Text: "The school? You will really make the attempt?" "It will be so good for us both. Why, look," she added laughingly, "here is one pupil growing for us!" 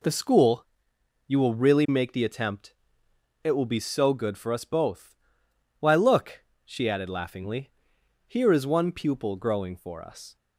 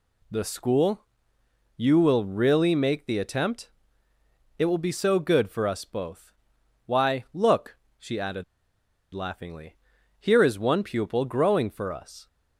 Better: first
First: none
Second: pauses between "added" and "laughingly"; noticeable; at 8.4 s; 0.69 s long

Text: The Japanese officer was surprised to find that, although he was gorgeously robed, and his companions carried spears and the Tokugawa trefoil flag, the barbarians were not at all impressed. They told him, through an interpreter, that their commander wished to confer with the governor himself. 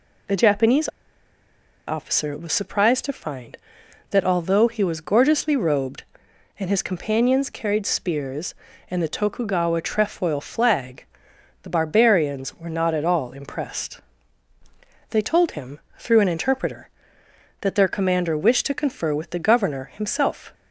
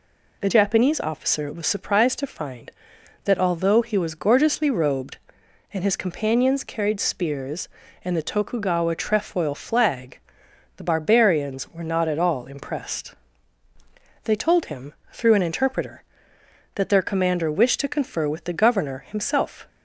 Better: second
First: pauses between "Japanese" and "officer"; at 0.8 s; 0.99 s long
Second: none

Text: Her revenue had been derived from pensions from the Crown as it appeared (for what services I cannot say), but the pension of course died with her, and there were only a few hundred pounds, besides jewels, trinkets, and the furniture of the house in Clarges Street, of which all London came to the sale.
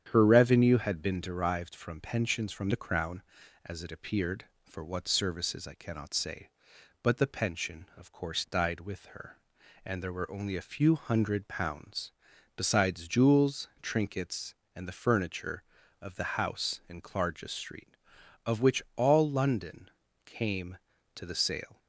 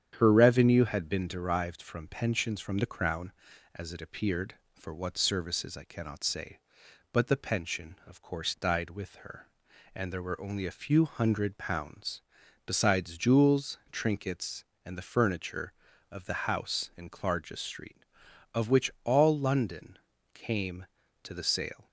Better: neither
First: starts louder than the rest; strong; until 1.1 s; 9 dB // pauses between "London" and "came"; at 19.8 s; 0.38 s long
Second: starts louder than the rest; strong; until 1.2 s; 9 dB // pauses between "London" and "came"; at 19.9 s; 0.38 s long

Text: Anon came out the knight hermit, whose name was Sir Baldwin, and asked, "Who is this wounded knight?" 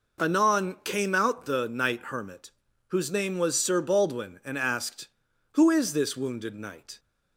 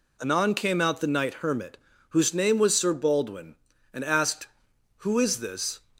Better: first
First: none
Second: stops before "wounded knight"; at 5.9 s

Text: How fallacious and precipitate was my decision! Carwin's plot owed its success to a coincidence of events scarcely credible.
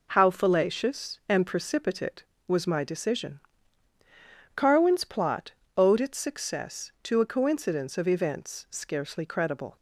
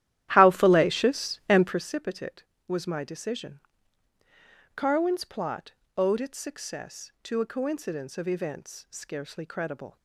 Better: first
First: pauses between "plot" and "owed"; slight; at 5.5 s; 0.26 s long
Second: starts louder than the rest; strong; until 1.9 s; 12.5 dB // pauses between "plot" and "owed"; slight; at 5.7 s; 0.26 s long

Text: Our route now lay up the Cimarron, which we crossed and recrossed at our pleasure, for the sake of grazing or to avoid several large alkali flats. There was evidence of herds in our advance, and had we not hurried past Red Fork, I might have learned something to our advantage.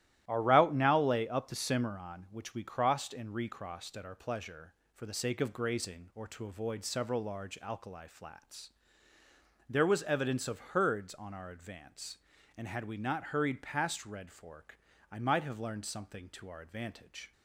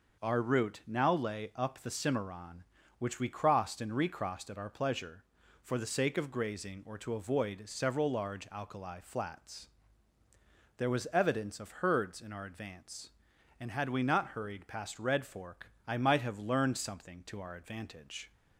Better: second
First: starts louder than the rest; strong; until 1.2 s; 13.5 dB // says "on" for "in"; at 11.1 s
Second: none

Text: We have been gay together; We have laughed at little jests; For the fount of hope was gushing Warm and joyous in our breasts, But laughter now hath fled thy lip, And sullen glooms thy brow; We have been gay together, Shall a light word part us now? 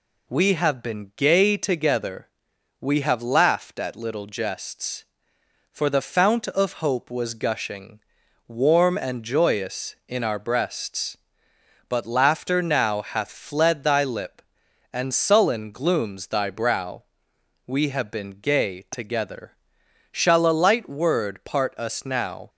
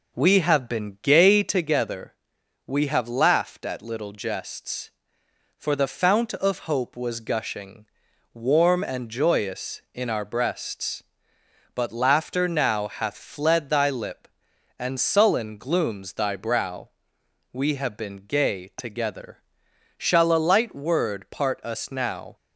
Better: first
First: pauses between "gushing" and "Warm"; noticeable; at 7.9 s; 0.48 s long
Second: starts louder than the rest; noticeable; until 1.7 s; 5.5 dB // pauses between "gushing" and "Warm"; noticeable; at 7.8 s; 0.48 s long

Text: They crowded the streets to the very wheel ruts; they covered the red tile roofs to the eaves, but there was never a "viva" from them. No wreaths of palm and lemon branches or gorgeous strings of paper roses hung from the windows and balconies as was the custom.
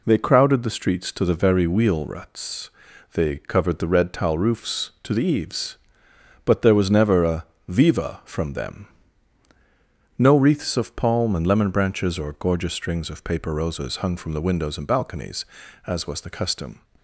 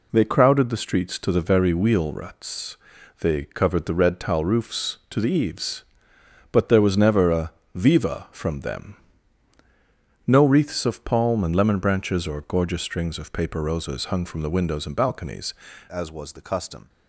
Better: first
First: pauses between "a" and "viva"; slight; at 7.4 s; 0.24 s long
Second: pauses between "a" and "viva"; slight; at 7.5 s; 0.24 s long // changes voice at "as"; from 15.8 s on; 1.0 s long

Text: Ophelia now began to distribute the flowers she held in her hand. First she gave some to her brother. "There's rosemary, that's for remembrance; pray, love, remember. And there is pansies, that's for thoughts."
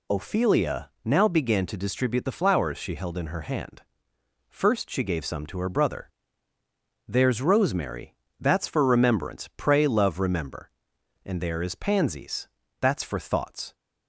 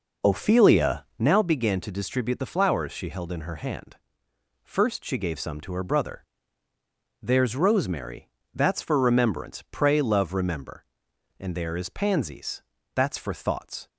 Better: first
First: none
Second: starts louder than the rest; noticeable; until 1.4 s; 5 dB

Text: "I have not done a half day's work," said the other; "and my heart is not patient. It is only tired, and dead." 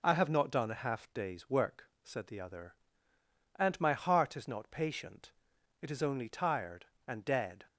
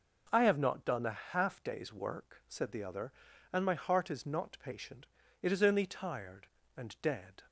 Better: neither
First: none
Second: none

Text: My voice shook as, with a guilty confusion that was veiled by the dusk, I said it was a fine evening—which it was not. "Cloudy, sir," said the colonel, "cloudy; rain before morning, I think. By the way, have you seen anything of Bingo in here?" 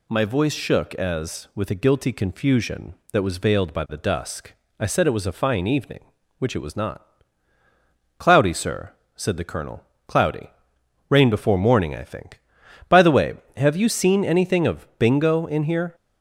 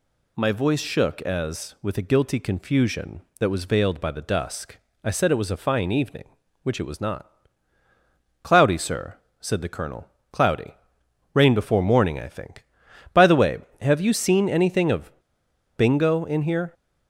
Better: first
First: none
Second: pauses between "of" and "Bingo"; noticeable; at 15.0 s; 0.68 s long

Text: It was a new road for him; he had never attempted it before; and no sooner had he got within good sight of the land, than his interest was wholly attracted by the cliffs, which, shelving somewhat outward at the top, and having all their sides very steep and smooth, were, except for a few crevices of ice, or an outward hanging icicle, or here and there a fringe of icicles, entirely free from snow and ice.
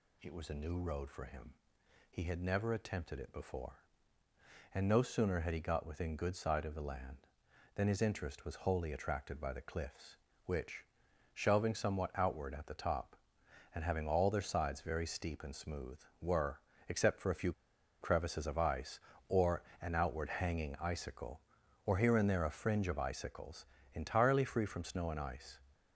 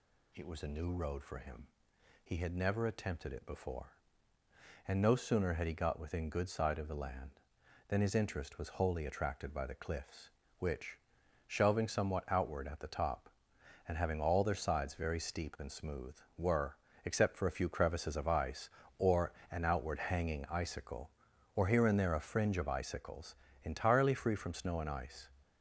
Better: second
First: pauses between "few" and "crevices"; noticeable; at 17.5 s; 0.47 s long // pauses between "or" and "an"; slight; at 19.6 s; 0.20 s long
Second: pauses between "or" and "an"; slight; at 19.3 s; 0.20 s long

